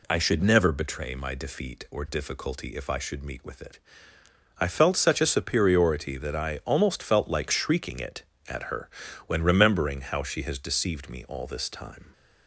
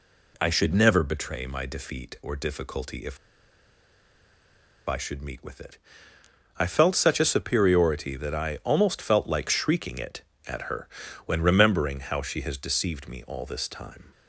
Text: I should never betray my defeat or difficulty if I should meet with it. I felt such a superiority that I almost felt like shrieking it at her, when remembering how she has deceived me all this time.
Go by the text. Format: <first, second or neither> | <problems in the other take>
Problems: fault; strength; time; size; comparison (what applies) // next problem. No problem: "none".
first | pauses between "if" and "I"; strong; at 3.1 s; 1.6 s long